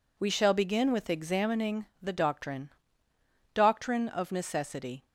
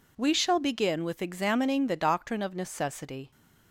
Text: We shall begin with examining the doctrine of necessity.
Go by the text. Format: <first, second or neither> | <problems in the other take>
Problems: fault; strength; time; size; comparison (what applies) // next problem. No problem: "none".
second | says "doctrine" twice; at 3.5 s